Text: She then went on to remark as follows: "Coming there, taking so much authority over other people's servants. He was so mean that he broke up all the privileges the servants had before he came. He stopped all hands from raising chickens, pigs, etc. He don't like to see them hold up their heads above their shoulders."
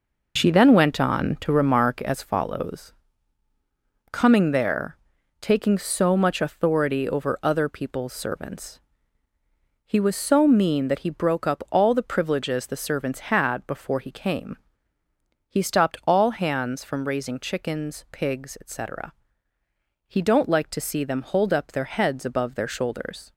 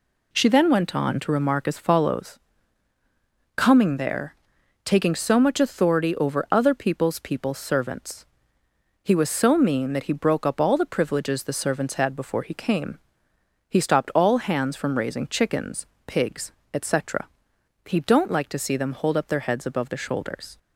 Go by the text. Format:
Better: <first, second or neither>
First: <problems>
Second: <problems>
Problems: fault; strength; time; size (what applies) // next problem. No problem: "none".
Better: first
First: none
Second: says "people's" twice; at 7.1 s